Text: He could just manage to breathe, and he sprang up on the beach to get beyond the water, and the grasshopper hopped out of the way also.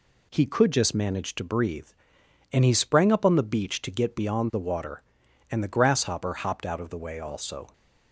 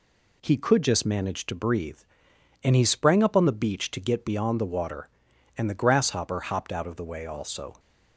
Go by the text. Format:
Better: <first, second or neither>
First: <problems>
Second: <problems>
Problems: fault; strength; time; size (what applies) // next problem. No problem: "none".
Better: neither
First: none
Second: none